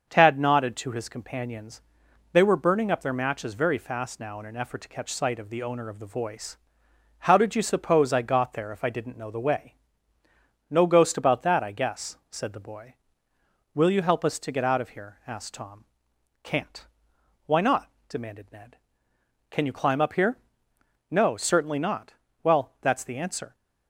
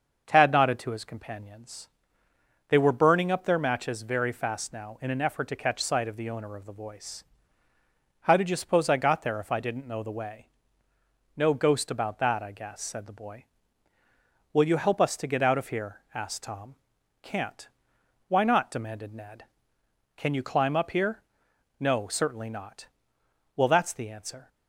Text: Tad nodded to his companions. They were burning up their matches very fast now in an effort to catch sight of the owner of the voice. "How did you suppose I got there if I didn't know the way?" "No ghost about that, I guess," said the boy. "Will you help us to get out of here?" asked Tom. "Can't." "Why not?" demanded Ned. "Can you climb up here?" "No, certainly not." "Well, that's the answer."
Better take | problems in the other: neither | starts louder than the rest; the same in both

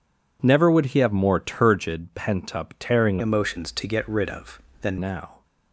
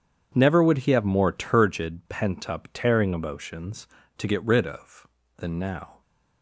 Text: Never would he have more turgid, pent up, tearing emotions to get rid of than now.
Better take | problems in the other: second | changes voice from "emotions" to "than"; from 3.1 to 4.9 s; 1.8 s long

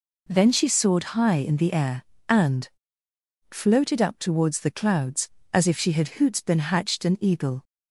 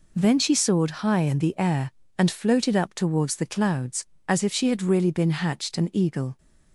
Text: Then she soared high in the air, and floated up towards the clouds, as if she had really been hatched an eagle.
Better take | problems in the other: second | pauses between "and" and "floated"; noticeable; at 2.6 s; 0.84 s long // says "hoots" for "really"; at 6.1 s

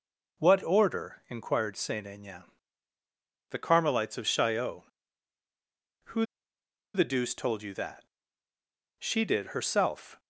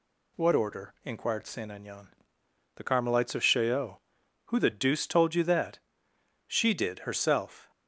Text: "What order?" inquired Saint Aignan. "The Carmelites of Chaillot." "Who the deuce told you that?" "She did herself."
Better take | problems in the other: second | pauses between "Who" and "the"; noticeable; at 6.2 s; 0.69 s long

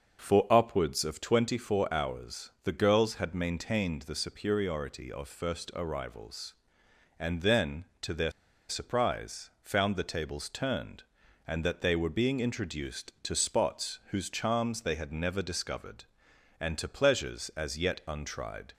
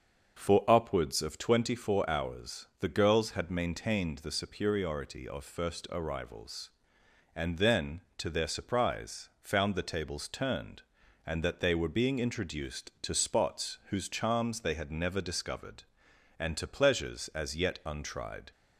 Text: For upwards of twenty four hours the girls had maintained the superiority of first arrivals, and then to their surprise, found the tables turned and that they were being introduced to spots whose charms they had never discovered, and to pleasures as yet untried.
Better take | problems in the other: second | starts louder than the rest; until 1.2 s; 6.5 dB; also in the second // pauses between "their" and "surprise"; at 8.2 s; 0.39 s long

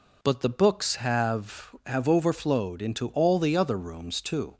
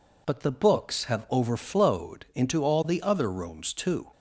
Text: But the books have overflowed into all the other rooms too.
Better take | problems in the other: second | says "have" twice; at 1.8 s

